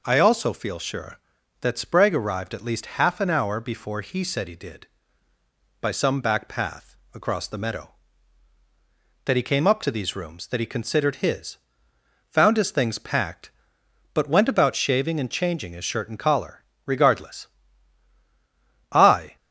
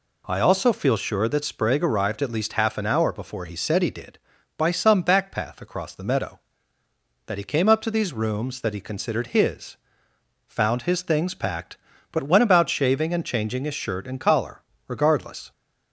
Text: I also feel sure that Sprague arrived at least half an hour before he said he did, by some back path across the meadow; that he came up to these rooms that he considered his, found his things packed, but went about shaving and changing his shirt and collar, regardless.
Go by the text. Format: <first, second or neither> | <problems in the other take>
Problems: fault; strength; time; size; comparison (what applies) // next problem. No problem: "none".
second | pauses between "path" and "across"; slight; at 6.9 s; 0.18 s long // goes on to say "I"; slight; from 18.8 s on; 0.46 s long